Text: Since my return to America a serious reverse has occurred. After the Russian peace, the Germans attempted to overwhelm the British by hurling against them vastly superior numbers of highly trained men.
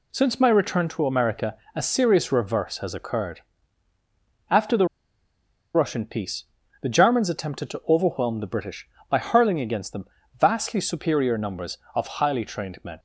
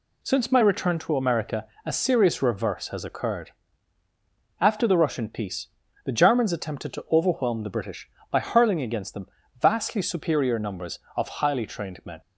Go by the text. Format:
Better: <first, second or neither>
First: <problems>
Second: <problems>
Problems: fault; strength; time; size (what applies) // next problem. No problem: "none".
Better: second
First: pauses between "America" and "a"; slight; at 1.5 s; 0.20 s long // pauses between "the" and "Russian"; noticeable; at 4.8 s; 0.87 s long // pauses between "them" and "vastly"; slight; at 10.0 s; 0.34 s long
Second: pauses between "America" and "a"; slight; at 1.6 s; 0.20 s long // pauses between "them" and "vastly"; slight; at 9.2 s; 0.34 s long